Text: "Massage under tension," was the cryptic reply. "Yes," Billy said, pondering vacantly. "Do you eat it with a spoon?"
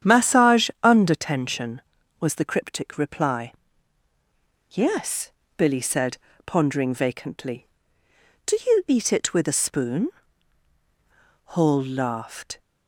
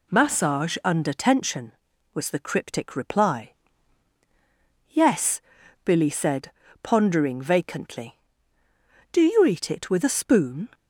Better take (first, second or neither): second